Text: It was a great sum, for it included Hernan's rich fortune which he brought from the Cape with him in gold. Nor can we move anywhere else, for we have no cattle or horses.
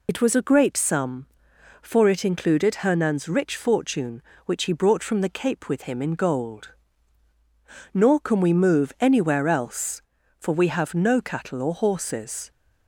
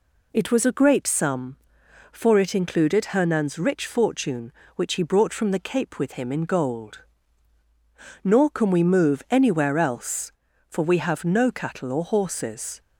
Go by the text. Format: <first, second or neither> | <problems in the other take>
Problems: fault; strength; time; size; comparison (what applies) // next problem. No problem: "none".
second | loses the start of "It"; at 0.0 s; 65 ms